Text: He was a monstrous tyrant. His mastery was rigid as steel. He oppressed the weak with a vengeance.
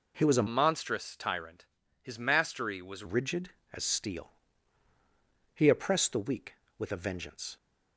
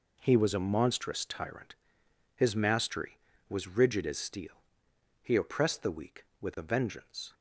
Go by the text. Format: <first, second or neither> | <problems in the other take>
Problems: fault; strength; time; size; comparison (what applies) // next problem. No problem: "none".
second | changes voice from "monstrous" to "was"; from 0.4 to 3.0 s; 2.6 s long